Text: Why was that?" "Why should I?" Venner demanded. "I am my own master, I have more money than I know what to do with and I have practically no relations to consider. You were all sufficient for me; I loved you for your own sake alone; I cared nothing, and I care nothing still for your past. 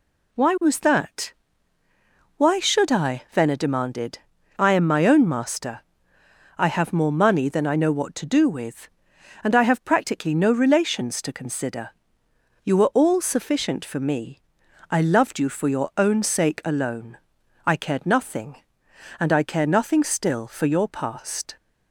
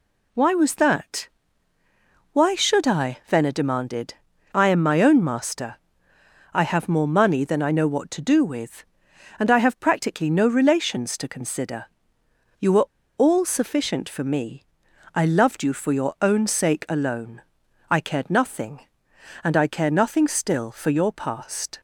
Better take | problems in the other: first | pauses between "were" and "all"; slight; at 12.8 s; 0.30 s long

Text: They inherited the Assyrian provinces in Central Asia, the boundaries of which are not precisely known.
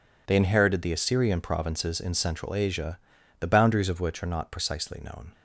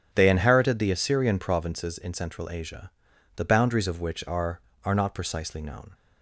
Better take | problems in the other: first | starts louder than the rest; strong; until 1.1 s; 8.5 dB // says "are" twice; at 4.8 s

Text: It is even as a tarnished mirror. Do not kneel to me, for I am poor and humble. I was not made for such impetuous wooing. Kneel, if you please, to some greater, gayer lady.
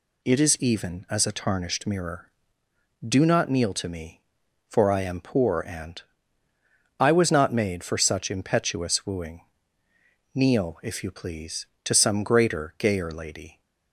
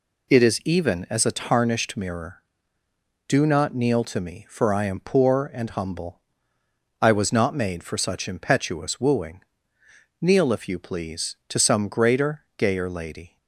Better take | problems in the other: second | skips "humble"; at 6.4 s

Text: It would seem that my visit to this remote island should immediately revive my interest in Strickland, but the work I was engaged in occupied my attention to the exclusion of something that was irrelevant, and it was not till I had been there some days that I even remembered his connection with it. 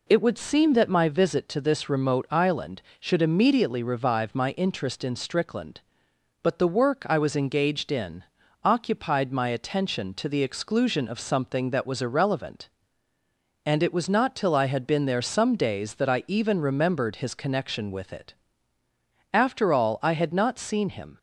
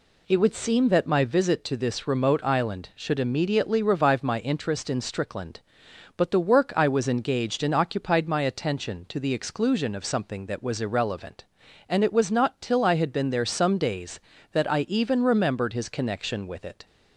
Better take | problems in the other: second | pauses between "in" and "occupied"; at 8.2 s; 0.40 s long // goes on to say "After all I had not seen him"; strong; from 19.3 s on; 1.8 s long

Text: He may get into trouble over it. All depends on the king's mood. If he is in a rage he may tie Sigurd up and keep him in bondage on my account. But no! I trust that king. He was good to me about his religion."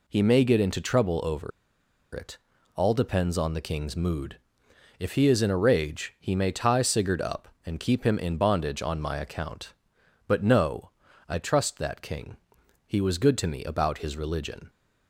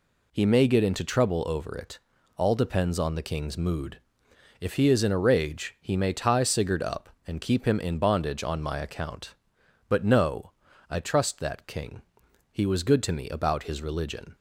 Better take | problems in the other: second | pauses between "over" and "it"; noticeable; at 1.5 s; 0.65 s long

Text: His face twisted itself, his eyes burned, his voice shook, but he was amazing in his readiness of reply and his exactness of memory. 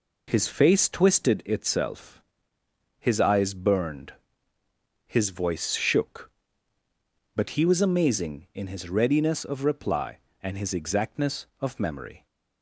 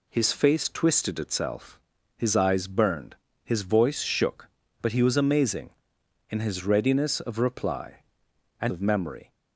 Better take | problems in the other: first | skips "his exactness"; at 8.7 s

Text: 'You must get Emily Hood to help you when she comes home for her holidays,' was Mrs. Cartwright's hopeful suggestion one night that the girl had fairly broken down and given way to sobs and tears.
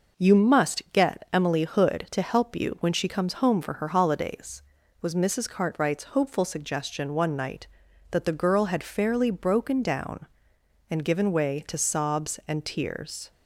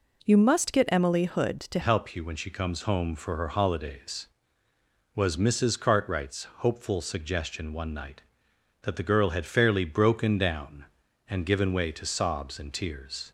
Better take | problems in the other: first | changes voice at "help"; from 1.8 s on; 11.5 s long

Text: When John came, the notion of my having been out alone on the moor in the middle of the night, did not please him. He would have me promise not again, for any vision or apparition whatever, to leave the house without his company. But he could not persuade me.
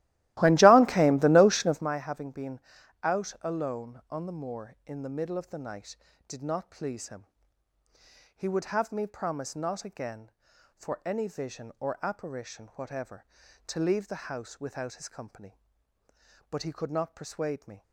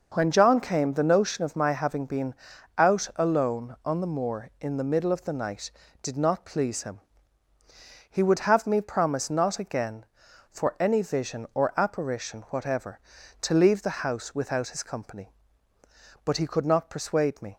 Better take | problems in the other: second | starts louder than the rest; strong; until 1.9 s; 16.5 dB // pauses between "been" and "out"; at 2.6 s; 0.42 s long; also in the second

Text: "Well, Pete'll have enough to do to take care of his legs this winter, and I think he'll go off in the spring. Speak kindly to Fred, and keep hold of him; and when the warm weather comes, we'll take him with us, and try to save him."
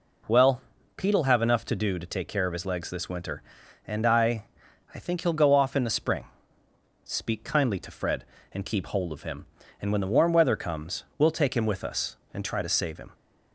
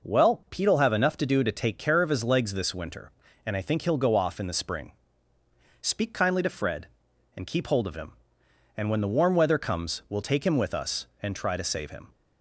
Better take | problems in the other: second | says "I" twice; at 4.9 s

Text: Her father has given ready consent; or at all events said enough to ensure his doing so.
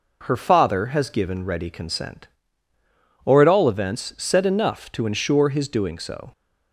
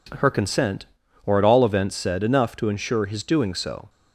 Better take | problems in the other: first | skips "father has given ready"; at 0.2 s

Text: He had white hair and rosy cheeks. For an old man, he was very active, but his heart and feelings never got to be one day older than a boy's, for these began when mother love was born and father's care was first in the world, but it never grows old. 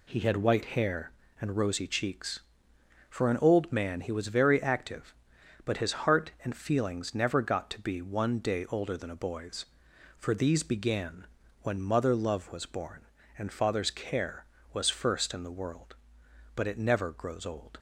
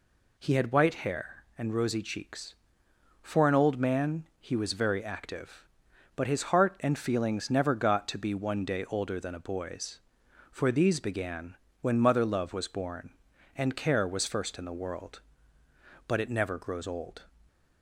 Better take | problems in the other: first | pauses between "began" and "when"; slight; at 11.5 s; 0.24 s long; slight in the first // skips "father's"; at 13.7 s

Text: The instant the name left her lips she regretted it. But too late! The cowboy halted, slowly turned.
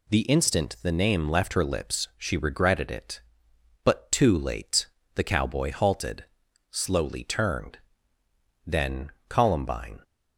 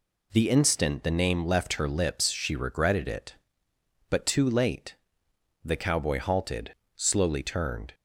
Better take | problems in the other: second | goes on to say "Then Columbine"; from 8.6 s on; 1.3 s long

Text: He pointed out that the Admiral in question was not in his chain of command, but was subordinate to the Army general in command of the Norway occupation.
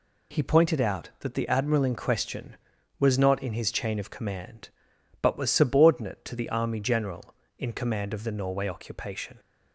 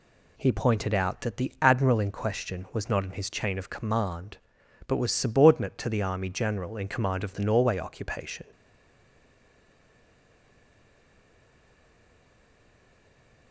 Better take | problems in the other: first | stays silent after the last word; strong; from 8.5 s on; 5.0 s long

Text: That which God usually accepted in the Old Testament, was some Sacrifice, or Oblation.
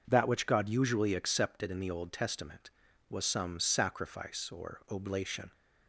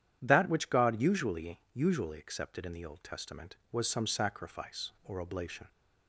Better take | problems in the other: first | starts louder than the rest; strong; until 1.2 s; 10 dB // says "usually" twice; at 1.7 s

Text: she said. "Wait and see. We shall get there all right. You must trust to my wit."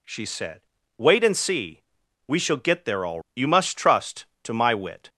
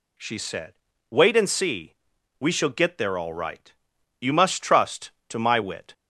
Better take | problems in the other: second | skips "right"; at 3.2 s

